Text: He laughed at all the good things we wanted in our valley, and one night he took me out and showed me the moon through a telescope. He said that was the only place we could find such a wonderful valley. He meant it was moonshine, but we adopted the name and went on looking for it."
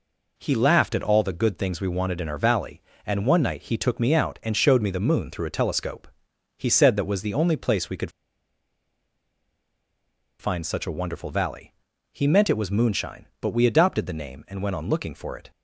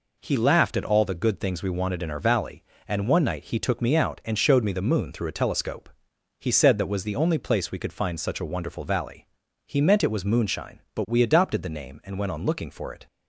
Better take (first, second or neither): second